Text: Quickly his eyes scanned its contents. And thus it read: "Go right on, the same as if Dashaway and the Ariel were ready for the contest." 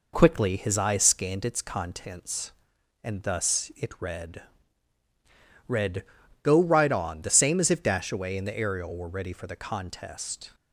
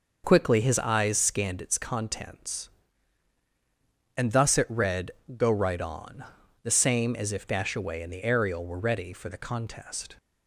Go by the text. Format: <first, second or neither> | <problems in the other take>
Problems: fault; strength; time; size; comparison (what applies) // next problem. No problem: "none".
second | says "read" twice; at 5.6 s